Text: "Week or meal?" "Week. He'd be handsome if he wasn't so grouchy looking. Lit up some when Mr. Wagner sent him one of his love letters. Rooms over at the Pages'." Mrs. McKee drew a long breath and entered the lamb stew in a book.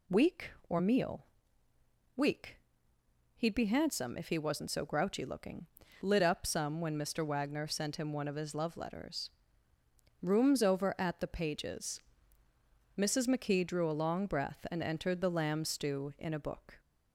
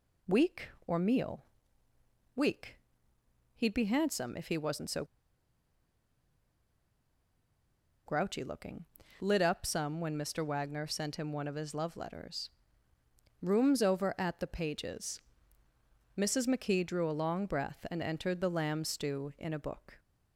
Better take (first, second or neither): first